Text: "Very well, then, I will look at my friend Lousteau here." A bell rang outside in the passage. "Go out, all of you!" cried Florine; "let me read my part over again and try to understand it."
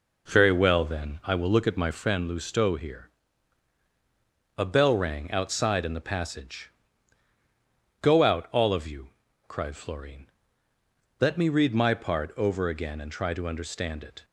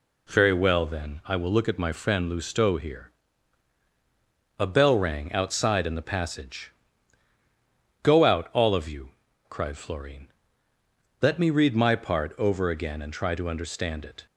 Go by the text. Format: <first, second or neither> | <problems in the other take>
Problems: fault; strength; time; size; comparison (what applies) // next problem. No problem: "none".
second | starts louder than the rest; noticeable; until 2.1 s; 4 dB